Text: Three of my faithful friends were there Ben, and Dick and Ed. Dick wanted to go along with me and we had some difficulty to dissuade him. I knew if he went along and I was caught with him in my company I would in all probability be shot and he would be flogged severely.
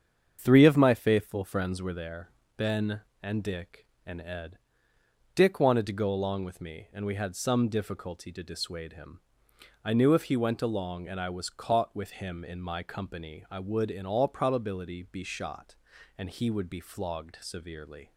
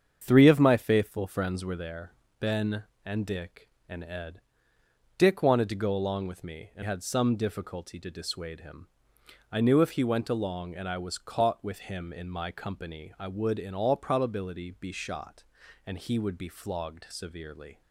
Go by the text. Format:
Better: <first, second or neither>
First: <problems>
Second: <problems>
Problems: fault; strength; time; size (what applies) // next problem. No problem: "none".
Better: first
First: starts louder than the rest; strong; until 1.4 s; 7.5 dB // pauses between "there" and "Ben"; slight; at 2.2 s; 0.26 s long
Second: starts louder than the rest; strong; until 1.2 s; 7.5 dB // pauses between "there" and "Ben"; slight; at 2.1 s; 0.26 s long // skips "we"; at 6.8 s